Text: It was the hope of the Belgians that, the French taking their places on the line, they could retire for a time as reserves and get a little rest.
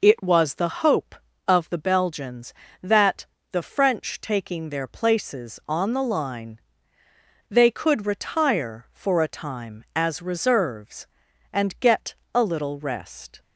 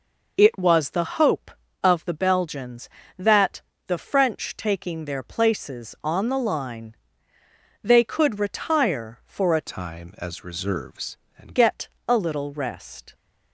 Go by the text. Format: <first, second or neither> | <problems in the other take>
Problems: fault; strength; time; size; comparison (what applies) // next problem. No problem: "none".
first | changes voice from "time" to "and"; from 9.6 to 11.5 s; 1.9 s long // pauses between "get" and "a"; slight; at 11.8 s; 0.18 s long; slight in the first